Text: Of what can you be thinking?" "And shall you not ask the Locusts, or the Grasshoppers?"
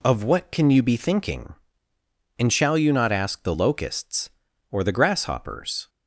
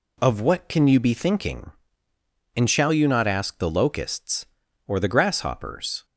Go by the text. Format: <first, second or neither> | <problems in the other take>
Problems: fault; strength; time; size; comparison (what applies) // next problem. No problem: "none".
neither | none